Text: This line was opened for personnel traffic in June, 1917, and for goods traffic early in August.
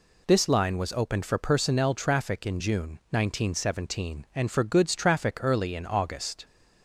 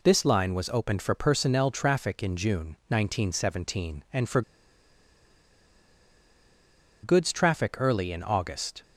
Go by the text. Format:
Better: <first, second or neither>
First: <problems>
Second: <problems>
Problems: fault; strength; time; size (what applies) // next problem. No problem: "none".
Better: first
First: none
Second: pauses between "for" and "goods"; strong; at 4.4 s; 2.6 s long